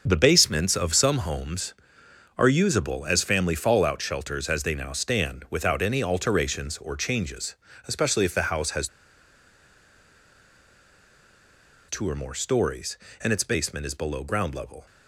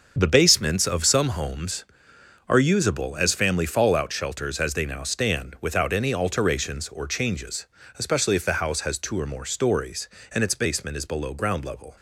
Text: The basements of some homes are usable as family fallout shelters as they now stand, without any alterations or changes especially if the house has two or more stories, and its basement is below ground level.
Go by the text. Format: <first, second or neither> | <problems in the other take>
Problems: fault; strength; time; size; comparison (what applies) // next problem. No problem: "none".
second | starts louder than the rest; until 1.0 s; 6.5 dB; also in the second // pauses between "changes" and "especially"; slight; at 7.5 s; 0.32 s long; slight in the second // pauses between "has" and "two"; strong; at 8.8 s; 3.0 s long